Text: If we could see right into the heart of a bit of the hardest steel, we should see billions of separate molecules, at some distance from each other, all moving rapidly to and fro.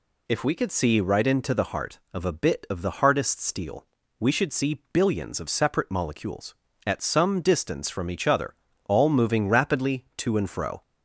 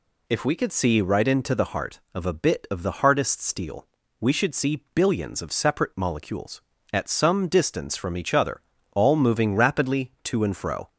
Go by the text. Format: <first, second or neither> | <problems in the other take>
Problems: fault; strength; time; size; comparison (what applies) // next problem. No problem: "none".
neither | none